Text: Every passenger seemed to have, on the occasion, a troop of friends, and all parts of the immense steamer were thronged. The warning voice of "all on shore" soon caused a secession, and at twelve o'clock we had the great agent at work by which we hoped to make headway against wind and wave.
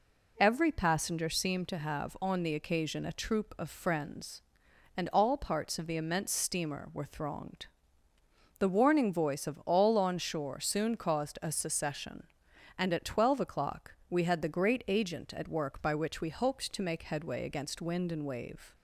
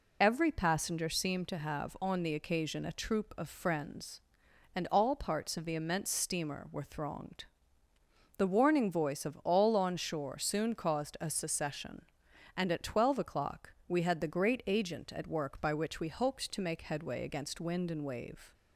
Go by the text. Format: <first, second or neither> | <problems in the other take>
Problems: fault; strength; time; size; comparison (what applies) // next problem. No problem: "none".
first | loses the start of "Every"; at 0.2 s; 35 ms